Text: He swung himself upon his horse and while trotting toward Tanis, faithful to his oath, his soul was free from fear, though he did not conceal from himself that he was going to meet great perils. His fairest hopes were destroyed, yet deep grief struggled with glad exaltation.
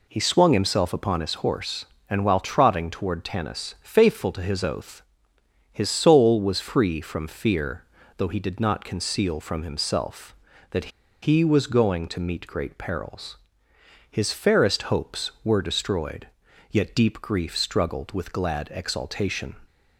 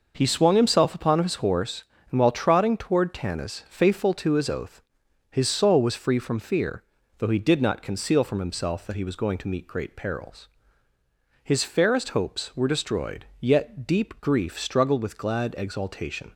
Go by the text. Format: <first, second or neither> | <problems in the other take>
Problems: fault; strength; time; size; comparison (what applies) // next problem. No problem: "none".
second | pauses between "that" and "he"; slight; at 10.9 s; 0.33 s long